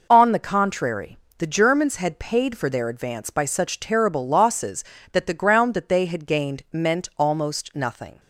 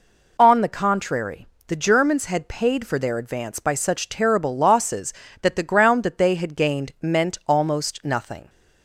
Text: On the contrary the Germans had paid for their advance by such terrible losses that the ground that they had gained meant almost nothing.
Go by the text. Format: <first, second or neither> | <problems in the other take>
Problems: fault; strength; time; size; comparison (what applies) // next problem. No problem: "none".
second | gets quieter; strong; throughout; 7.5 dB // pauses between "contrary" and "the"; slight; at 1.1 s; 0.22 s long; slight in the second